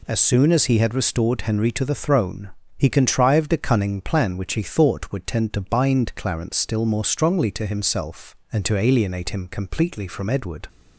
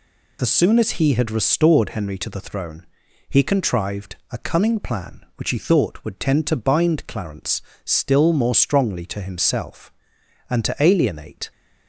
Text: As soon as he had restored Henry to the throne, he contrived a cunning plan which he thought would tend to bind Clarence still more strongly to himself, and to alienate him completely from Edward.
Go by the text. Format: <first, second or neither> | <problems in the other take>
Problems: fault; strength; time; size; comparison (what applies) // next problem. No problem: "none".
first | pauses between "Clarence" and "still"; slight; at 7.6 s; 0.24 s long // stops before "him completely from Edward"; at 11.5 s